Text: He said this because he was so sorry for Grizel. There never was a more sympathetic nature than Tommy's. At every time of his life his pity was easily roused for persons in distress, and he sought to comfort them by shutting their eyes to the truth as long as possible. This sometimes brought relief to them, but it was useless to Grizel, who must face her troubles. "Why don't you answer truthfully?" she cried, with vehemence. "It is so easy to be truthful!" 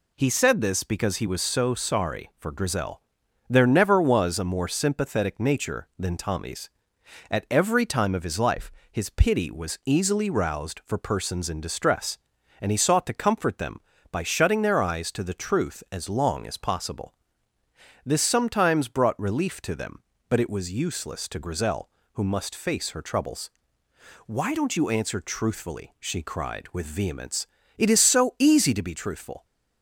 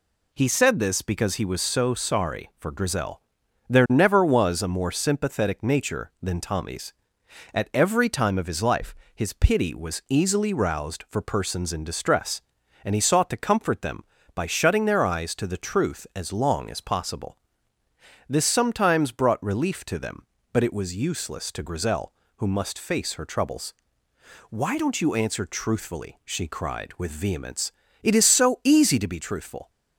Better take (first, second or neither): neither